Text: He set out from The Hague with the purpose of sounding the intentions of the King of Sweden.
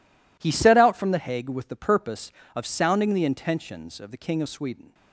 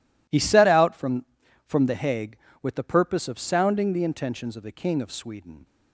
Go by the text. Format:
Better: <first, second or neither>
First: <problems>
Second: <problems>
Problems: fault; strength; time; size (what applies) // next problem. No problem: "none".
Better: first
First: none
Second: says "from" twice; at 1.6 s